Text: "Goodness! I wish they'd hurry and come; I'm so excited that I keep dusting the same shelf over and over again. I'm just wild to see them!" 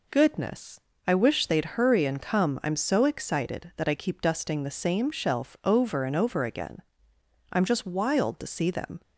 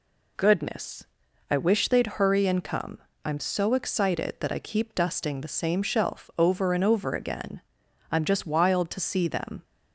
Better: neither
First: none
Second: none

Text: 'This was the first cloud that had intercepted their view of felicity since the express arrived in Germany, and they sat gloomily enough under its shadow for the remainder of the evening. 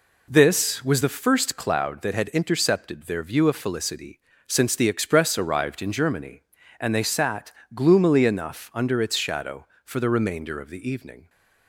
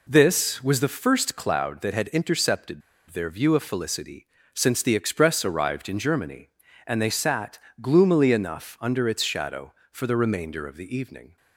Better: first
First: pauses between "felicity" and "since"; slight; at 4.1 s; 0.26 s long // pauses between "sat" and "gloomily"; slight; at 7.5 s; 0.20 s long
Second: pauses between "intercepted" and "their"; slight; at 2.8 s; 0.29 s long // pauses between "felicity" and "since"; slight; at 4.2 s; 0.26 s long // pauses between "sat" and "gloomily"; slight; at 7.6 s; 0.20 s long

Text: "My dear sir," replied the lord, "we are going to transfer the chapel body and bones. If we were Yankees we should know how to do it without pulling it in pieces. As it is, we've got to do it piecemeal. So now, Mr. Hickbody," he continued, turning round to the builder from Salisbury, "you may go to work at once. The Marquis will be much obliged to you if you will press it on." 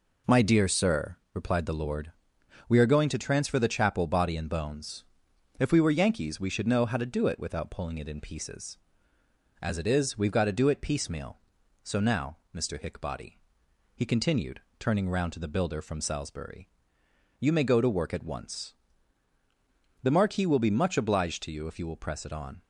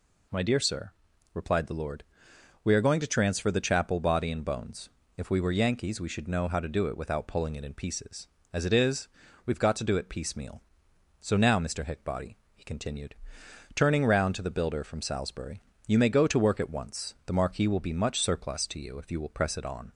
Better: first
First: none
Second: says "surplus" for "obliged"; at 18.1 s

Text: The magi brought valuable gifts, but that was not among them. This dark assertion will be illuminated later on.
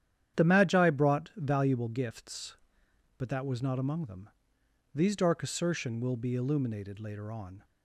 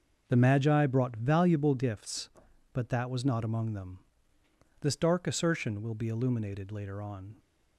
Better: second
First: starts louder than the rest; strong; until 1.4 s; 10 dB // says "These" for "This"; at 4.9 s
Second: none

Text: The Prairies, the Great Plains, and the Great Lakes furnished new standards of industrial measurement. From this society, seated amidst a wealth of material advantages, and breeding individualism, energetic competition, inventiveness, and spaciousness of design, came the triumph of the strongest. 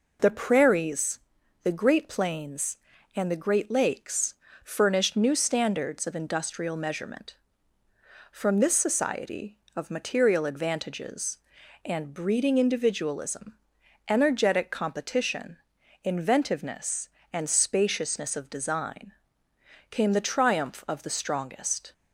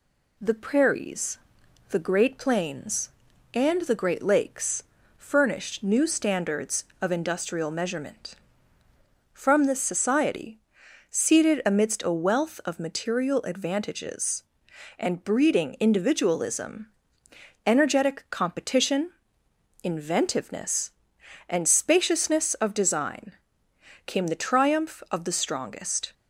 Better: second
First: pauses between "Lakes" and "furnished"; slight; at 4.3 s; 0.28 s long // skips "seated amidst a wealth"; at 9.6 s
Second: pauses between "Lakes" and "furnished"; slight; at 4.8 s; 0.34 s long

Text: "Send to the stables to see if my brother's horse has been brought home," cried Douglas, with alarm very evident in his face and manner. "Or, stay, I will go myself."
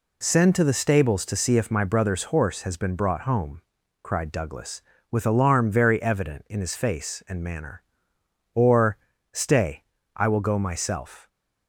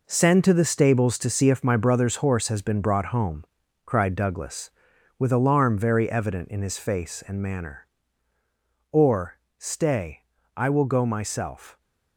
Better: first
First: none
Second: gets quieter; strong; throughout; 9 dB

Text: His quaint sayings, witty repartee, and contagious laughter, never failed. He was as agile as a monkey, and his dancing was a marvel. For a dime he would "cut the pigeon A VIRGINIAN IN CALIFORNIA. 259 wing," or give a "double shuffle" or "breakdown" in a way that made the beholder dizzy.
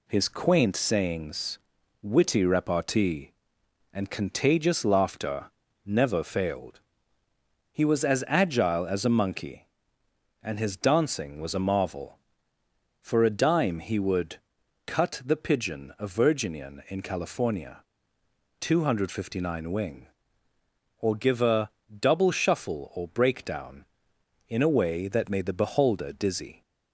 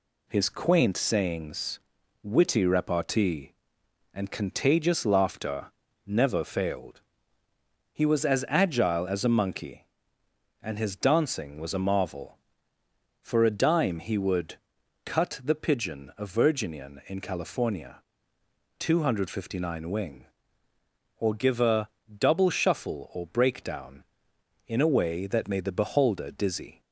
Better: neither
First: pauses between "would" and "cut"; noticeable; at 14.3 s; 0.48 s long // pauses between "a" and "double"; slight; at 21.7 s; 0.18 s long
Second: pauses between "would" and "cut"; noticeable; at 14.5 s; 0.48 s long // pauses between "a" and "double"; slight; at 21.8 s; 0.18 s long

